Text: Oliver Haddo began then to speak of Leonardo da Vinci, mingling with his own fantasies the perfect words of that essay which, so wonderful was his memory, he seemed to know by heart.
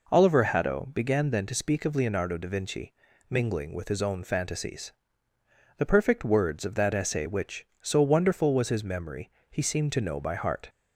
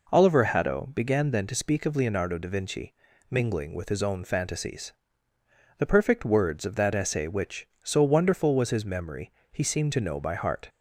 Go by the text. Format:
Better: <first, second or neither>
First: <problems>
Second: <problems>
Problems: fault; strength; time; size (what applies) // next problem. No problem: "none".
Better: neither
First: pauses between "fantasies" and "the"; noticeable; at 4.9 s; 0.86 s long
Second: pauses between "fantasies" and "the"; noticeable; at 4.9 s; 0.86 s long